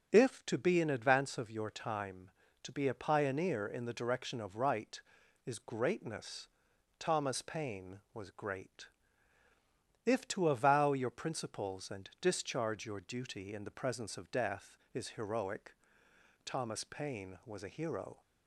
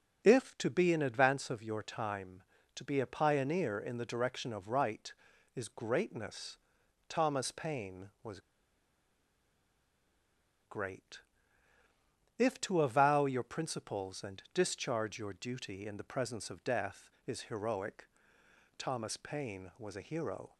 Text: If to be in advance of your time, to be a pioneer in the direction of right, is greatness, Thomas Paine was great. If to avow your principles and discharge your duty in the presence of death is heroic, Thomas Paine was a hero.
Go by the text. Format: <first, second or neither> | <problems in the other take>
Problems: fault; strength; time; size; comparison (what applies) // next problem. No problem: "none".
first | pauses between "was" and "great"; strong; at 8.4 s; 2.2 s long